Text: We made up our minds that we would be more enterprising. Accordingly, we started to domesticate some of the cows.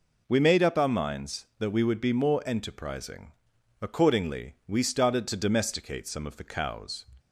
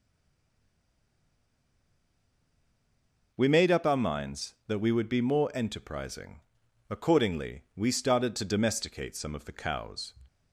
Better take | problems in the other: first | stays silent before the first word; strong; until 3.3 s; 3.3 s long

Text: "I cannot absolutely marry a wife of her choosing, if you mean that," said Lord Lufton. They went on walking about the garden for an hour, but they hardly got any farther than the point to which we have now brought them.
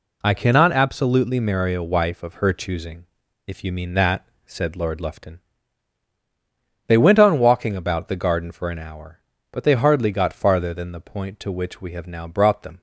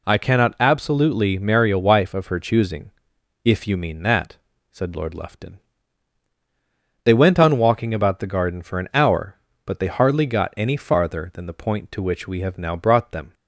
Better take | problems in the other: second | skips "any"; at 10.3 s

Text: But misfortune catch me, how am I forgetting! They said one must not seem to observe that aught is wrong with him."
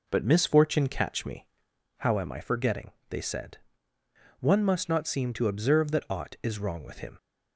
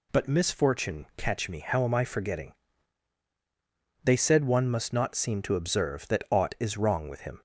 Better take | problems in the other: second | starts louder than the rest; noticeable; until 1.9 s; 4.5 dB // pauses between "said" and "one"; noticeable; at 3.5 s; 0.82 s long

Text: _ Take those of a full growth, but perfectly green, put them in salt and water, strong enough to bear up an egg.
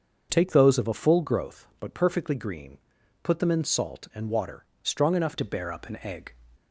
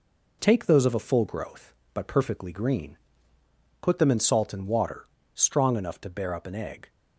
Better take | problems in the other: second | starts louder than the rest; until 1.3 s; 6.5 dB // changes voice at "to"; from 5.3 s on; 1.0 s long

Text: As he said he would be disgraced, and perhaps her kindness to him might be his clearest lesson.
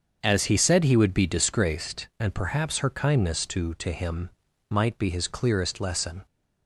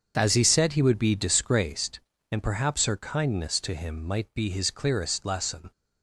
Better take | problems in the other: second | starts louder than the rest; until 1.2 s; 7 dB; also in the second // says "to" twice; at 3.7 s // pauses between "him" and "might"; at 4.2 s; 0.40 s long

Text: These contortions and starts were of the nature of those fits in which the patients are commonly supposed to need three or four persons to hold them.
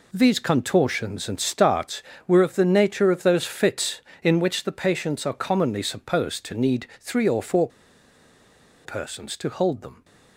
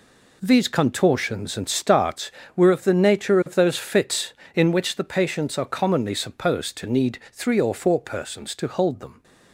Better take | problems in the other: second | pauses between "four" and "persons"; at 7.6 s; 1.1 s long

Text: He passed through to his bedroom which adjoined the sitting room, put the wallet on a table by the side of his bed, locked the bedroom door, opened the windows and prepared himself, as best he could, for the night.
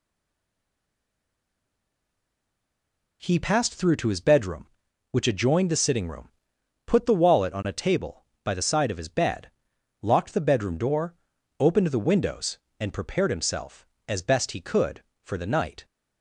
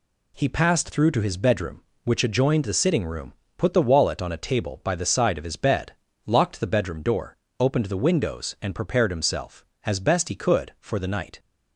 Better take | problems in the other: second | stays silent before the first word; strong; until 3.2 s; 3.2 s long

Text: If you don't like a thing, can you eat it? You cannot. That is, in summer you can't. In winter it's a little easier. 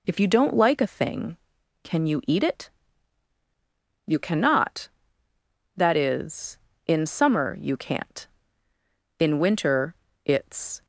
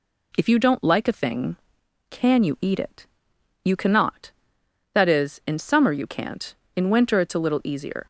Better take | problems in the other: second | pauses between "winter" and "it's"; slight; at 9.9 s; 0.30 s long // stops before "a little easier"; at 10.8 s

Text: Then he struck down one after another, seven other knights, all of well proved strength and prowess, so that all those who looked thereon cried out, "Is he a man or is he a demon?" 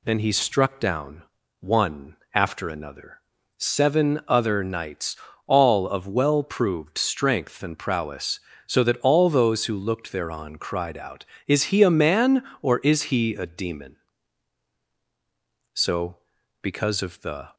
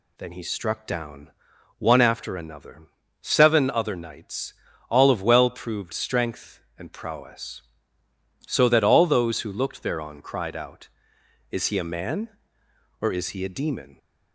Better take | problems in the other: second | pauses between "down" and "one"; at 1.2 s; 0.38 s long; noticeable in the second // pauses between "one" and "after"; slight; at 2.1 s; 0.18 s long // goes on to say "So because of the"; strong; from 15.7 s on; 1.8 s long

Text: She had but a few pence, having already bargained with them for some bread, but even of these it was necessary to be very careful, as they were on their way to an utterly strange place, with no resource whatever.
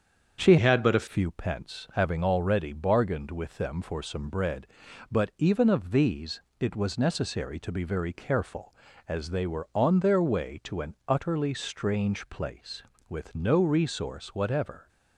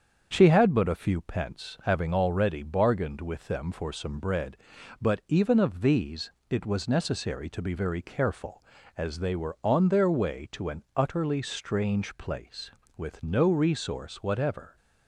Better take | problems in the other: second | starts louder than the rest; strong; until 1.4 s; 7.5 dB; strong in the second // changes voice from "had" to "a"; from 0.5 to 1.0 s; 0.5 s long // pauses between "these" and "it"; slight; at 6.3 s; 0.18 s long; slight in the second

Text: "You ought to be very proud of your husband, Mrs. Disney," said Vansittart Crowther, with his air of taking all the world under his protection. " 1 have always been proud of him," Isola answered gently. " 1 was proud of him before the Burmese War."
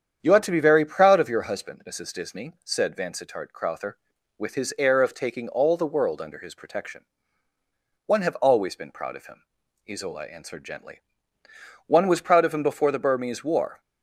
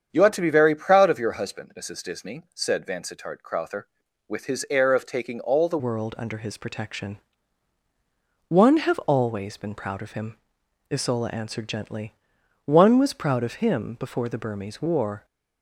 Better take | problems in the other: first | starts louder than the rest; strong; until 1.1 s; 8 dB; strong in the first // changes voice at "world"; from 5.7 s on; 9.5 s long

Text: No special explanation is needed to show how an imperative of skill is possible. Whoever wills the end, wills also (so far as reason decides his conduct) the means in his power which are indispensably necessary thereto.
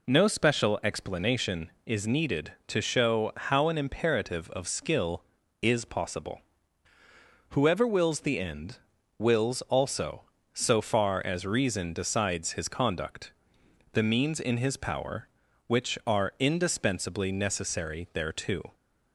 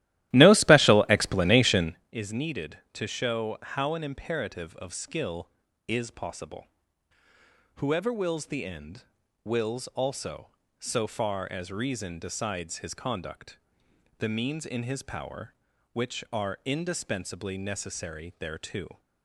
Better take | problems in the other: first | starts louder than the rest; strong; until 2.0 s; 15 dB

